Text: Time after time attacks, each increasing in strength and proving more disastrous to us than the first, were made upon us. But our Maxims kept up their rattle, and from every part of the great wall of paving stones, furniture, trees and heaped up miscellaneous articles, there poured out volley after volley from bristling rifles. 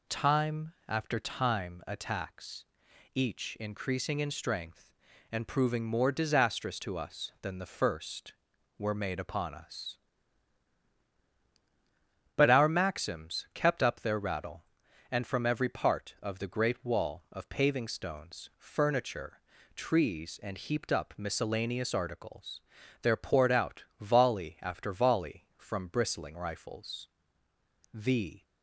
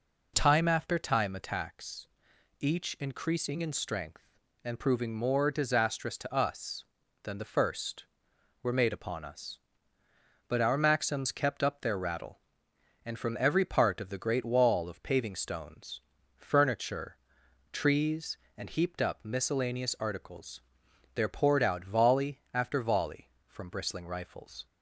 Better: second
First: goes on to say "The"; from 27.9 s on; 0.54 s long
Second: none

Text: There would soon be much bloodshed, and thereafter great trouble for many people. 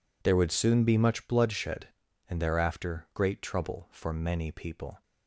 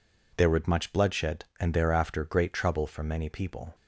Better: first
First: none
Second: skips "soon be"; at 0.6 s

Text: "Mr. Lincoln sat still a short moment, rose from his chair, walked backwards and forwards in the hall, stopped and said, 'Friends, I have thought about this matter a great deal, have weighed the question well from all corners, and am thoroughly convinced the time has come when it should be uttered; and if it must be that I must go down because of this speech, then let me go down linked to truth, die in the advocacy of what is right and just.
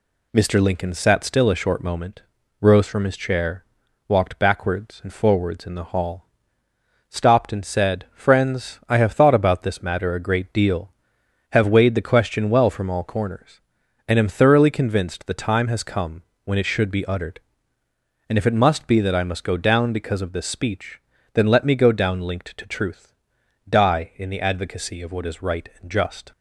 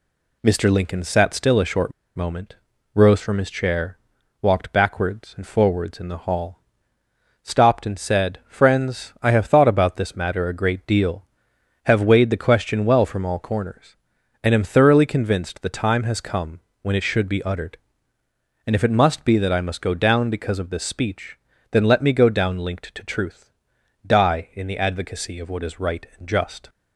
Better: first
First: pauses between "come" and "when"; slight; at 16.2 s; 0.20 s long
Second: pauses between "short" and "moment"; slight; at 1.9 s; 0.25 s long // pauses between "come" and "when"; slight; at 16.6 s; 0.20 s long

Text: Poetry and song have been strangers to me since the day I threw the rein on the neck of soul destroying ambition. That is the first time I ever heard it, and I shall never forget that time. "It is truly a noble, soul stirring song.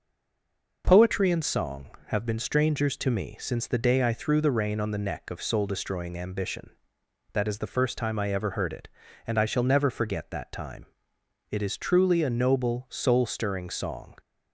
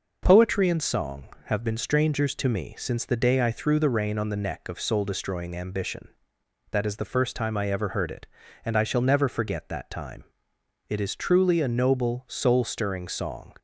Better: second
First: stays silent before the first word; slight; until 0.8 s; 0.8 s long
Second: none

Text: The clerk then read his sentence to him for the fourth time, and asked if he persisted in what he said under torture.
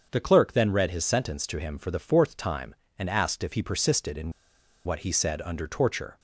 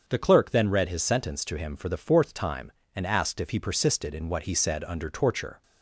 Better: second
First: starts louder than the rest; until 1.1 s; 7 dB // pauses between "in" and "what"; noticeable; at 4.3 s; 0.53 s long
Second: starts louder than the rest; until 1.0 s; 7 dB

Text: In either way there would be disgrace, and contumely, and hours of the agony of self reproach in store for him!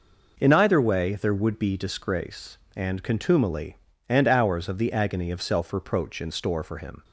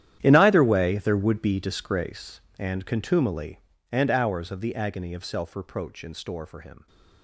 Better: first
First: none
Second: gets quieter; strong; throughout; 17 dB

